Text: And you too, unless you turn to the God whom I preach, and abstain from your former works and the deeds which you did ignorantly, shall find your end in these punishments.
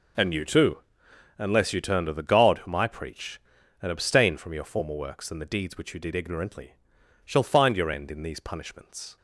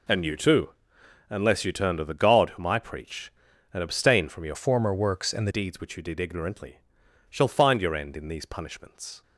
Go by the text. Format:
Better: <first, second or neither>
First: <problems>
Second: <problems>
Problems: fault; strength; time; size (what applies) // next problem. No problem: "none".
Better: first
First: none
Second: changes voice from "former" to "the"; from 4.5 to 5.5 s; 1.0 s long